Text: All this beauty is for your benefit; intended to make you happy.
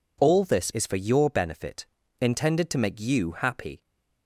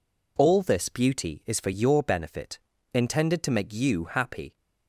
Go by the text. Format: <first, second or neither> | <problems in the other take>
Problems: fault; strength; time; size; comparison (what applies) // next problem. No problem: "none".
second | skips "beauty"; at 0.7 s